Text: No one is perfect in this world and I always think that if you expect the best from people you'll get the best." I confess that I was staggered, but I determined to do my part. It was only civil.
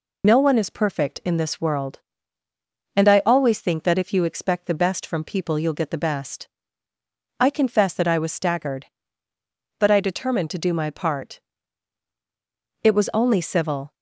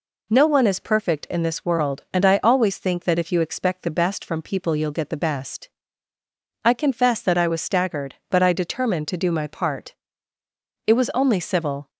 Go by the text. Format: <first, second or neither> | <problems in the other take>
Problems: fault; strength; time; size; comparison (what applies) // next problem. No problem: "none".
second | loses the start of "No"; at 0.2 s; 35 ms